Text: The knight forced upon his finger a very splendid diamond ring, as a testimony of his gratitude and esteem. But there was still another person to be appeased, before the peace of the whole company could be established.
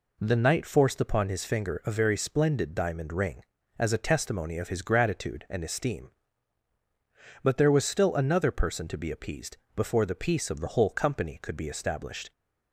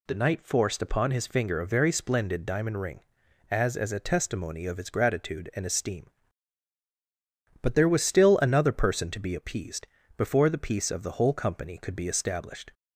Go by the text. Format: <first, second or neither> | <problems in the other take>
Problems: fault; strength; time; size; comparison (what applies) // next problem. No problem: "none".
first | says "as" twice; at 3.7 s